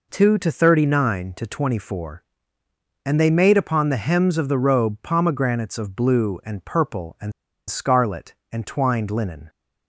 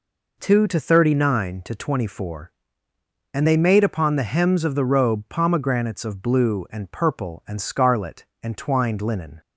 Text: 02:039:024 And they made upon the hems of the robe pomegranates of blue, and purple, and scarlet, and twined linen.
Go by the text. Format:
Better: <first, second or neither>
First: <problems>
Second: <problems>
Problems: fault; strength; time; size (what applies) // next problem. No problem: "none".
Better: second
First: pauses between "and" and "scarlet"; slight; at 7.3 s; 0.36 s long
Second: none